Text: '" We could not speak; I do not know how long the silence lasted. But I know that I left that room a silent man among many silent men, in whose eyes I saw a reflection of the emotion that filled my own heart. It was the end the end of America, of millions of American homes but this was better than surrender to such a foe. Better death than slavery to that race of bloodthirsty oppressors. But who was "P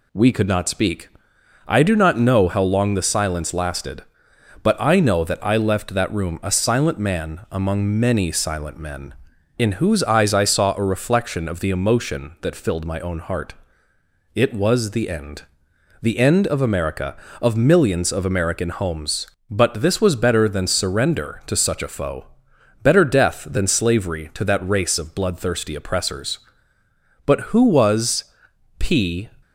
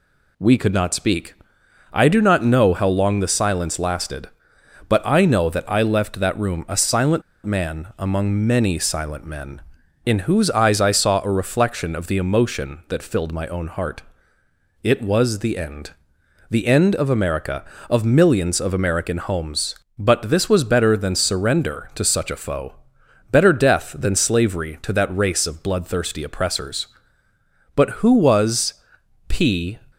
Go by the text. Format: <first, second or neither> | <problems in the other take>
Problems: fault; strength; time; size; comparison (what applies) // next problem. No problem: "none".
first | pauses between "silent" and "man"; slight; at 7.2 s; 0.23 s long // pauses between "end" and "the"; noticeable; at 15.9 s; 0.58 s long; noticeable in the first // pauses between "was" and "P"; noticeable; at 28.7 s; 0.54 s long; noticeable in the first